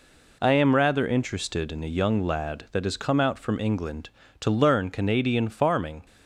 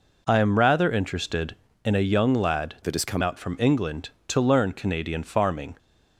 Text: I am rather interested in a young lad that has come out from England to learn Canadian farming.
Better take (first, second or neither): first